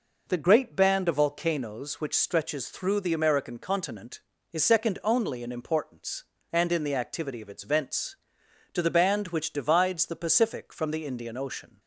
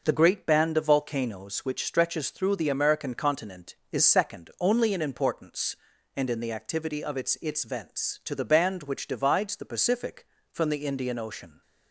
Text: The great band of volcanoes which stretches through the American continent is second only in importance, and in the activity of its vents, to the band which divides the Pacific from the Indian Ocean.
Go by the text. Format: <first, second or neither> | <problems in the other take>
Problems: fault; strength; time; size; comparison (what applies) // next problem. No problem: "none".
first | says "its" twice; at 7.4 s